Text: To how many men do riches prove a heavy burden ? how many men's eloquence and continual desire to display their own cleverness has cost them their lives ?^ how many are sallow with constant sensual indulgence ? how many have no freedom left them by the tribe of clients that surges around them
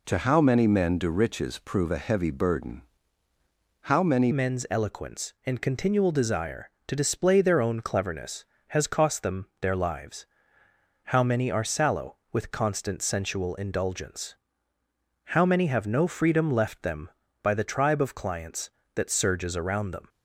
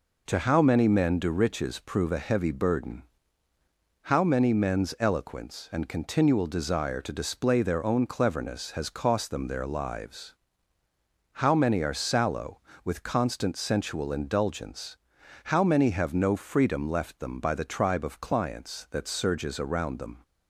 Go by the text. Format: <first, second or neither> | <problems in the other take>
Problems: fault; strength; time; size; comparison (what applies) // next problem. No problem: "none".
second | changes voice at "men's"; from 4.3 s on; 15.7 s long